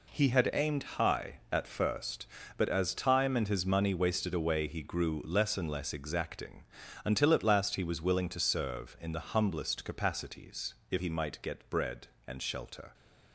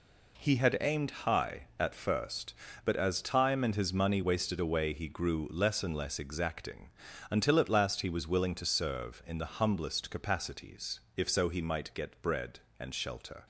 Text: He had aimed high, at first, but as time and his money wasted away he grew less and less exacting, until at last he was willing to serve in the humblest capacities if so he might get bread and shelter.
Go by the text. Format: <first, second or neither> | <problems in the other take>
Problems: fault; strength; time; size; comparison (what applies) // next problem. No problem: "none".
second | pauses between "capacities" and "if"; slight; at 10.7 s; 0.16 s long; slight in the second // skips "so"; at 10.9 s